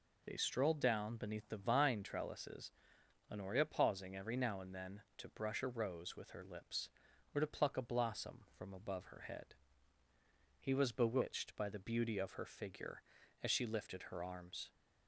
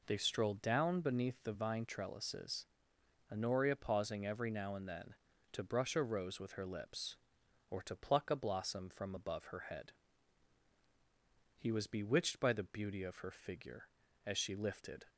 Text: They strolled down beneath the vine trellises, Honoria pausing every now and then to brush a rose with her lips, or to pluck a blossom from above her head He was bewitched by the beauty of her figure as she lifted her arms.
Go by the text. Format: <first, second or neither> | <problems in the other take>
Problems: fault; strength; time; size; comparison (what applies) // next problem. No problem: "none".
first | pauses between "head" and "He"; strong; at 9.9 s; 1.6 s long; also in the first // stops before "her arms"; at 15.0 s